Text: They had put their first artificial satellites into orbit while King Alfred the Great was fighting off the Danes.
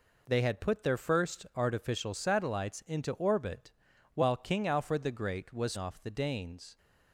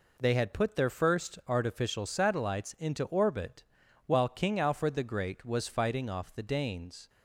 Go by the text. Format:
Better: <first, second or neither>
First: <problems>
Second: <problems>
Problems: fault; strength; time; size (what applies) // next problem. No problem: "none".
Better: second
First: pauses between "orbit" and "while"; at 3.7 s; 0.44 s long // skips "fighting"; at 5.7 s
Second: pauses between "orbit" and "while"; at 3.6 s; 0.44 s long